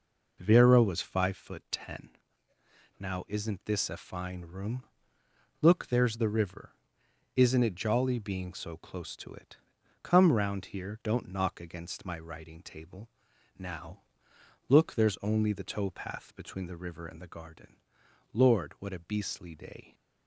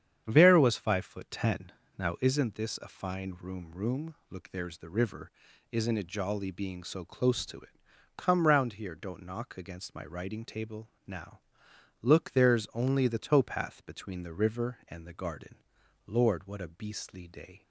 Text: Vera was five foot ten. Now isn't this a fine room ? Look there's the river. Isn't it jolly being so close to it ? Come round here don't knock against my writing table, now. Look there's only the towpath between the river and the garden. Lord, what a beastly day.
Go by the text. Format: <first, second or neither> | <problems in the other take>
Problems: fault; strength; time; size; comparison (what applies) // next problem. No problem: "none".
first | starts louder than the rest; strong; until 1.2 s; 8.5 dB // says "room" twice; at 3.7 s